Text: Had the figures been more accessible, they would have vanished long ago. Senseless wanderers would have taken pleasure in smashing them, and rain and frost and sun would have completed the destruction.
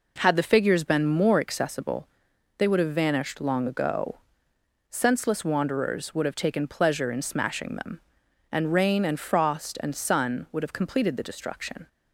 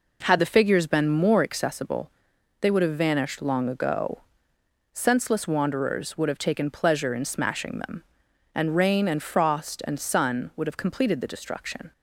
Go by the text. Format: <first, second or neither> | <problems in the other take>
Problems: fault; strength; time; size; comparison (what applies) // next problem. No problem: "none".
neither | none